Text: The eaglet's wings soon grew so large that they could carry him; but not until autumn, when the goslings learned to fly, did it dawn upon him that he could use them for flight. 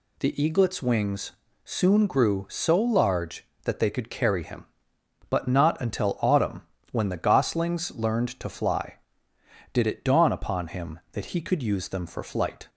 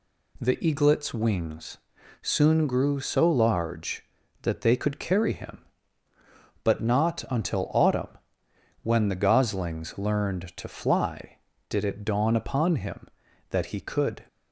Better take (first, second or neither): first